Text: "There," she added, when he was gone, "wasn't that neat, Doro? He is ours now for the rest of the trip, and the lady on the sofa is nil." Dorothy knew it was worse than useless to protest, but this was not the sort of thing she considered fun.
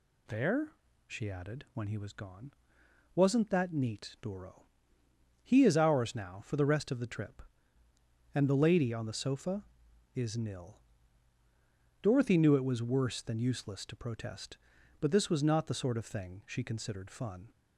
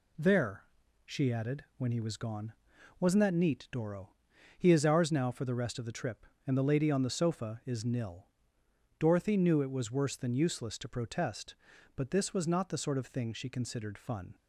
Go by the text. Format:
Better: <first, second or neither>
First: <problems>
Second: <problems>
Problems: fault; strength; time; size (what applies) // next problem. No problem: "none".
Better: first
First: none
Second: gets quieter; noticeable; throughout; 4.5 dB